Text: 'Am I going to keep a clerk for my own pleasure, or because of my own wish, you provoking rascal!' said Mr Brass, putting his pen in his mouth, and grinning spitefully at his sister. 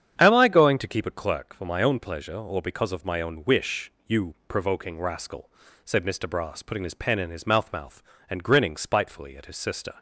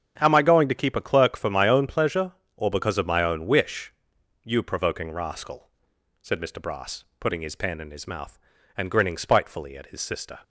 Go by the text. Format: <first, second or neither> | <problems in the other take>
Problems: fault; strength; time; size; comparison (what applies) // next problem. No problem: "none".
second | starts louder than the rest; strong; until 1.1 s; 8.5 dB; strong in the second // says "mouth" twice; at 7.7 s